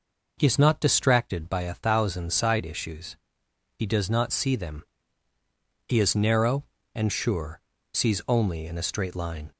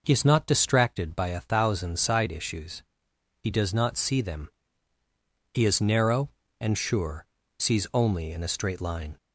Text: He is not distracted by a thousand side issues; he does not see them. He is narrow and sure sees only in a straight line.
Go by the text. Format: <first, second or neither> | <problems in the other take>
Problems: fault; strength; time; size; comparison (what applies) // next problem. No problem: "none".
neither | pauses between "sure" and "sees"; slight; the same in both